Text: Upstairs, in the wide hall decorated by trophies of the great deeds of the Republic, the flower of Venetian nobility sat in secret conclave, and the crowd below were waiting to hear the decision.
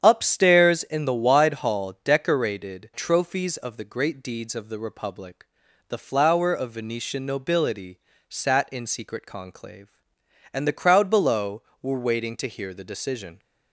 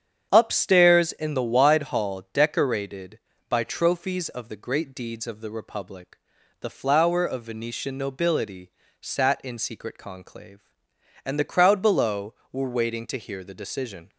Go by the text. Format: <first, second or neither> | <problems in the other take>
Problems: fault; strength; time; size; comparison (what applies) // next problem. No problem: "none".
second | starts louder than the rest; strong; until 1.0 s; 8 dB; strong in the second // skips "by"; at 2.9 s // pauses between "nobility" and "sat"; slight; at 7.9 s; 0.28 s long; slight in the second